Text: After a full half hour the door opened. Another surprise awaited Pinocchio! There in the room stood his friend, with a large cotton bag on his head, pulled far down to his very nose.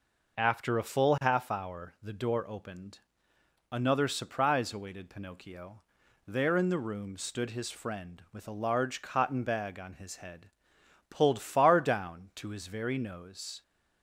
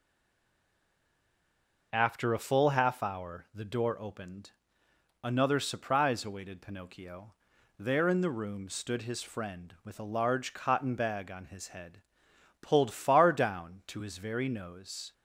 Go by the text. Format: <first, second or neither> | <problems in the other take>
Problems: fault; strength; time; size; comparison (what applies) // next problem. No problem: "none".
first | stays silent before the first word; noticeable; until 1.9 s; 1.9 s long